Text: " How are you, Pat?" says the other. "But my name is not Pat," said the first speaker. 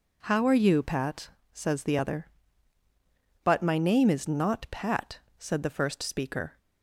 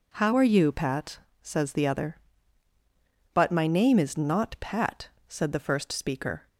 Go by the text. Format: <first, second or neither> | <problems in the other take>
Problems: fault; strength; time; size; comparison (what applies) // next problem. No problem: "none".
neither | none